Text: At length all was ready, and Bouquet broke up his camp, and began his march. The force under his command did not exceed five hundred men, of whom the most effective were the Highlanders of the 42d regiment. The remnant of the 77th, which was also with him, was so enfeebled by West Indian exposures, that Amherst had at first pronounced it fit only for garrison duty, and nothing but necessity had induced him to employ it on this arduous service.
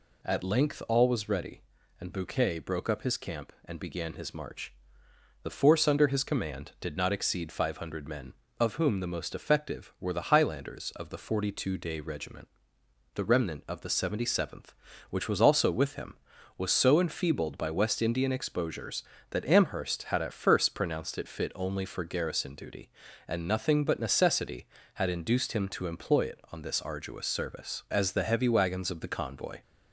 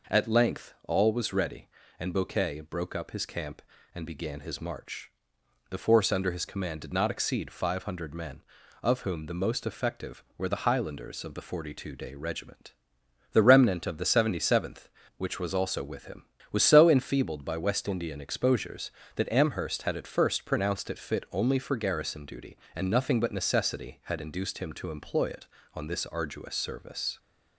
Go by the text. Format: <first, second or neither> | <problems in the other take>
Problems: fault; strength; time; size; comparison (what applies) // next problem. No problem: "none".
second | goes on to say "As the heavy wagons of the convoy"; strong; from 27.8 s on; 1.7 s long